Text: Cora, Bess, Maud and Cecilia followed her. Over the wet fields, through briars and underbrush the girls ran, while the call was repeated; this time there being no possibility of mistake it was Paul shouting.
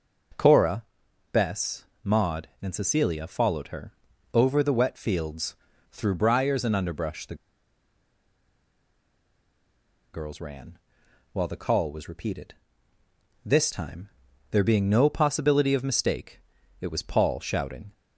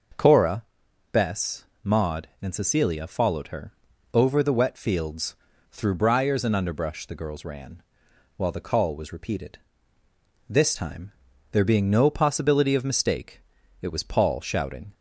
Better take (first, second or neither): second